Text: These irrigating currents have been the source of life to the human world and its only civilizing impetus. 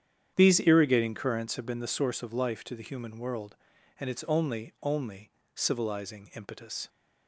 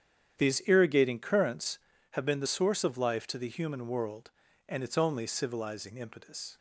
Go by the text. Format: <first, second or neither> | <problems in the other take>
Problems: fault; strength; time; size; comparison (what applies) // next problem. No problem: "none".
second | starts louder than the rest; strong; until 1.3 s; 9 dB; strong in the second // says "only" twice; at 4.8 s